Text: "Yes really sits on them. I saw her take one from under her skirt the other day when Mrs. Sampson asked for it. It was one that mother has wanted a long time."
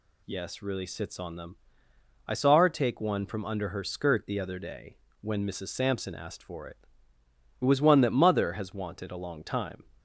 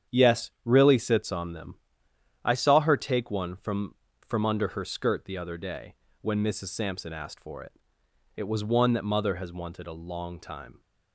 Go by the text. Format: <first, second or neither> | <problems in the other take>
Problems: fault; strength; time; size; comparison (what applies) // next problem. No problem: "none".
first | starts louder than the rest; strong; until 1.2 s; 8.5 dB // says "from" twice; at 4.2 s // pauses between "day" and "when"; slight; at 5.9 s; 0.26 s long; slight in the first